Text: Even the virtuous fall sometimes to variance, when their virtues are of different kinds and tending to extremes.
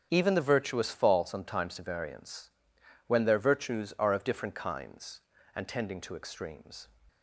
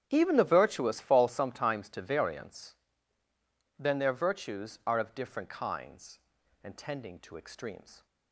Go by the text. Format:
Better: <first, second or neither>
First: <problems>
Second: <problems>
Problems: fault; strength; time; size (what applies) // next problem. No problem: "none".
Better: first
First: starts louder than the rest; strong; until 1.1 s; 8 dB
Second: starts louder than the rest; strong; until 1.1 s; 9.5 dB // says "then" for "when"; at 3.7 s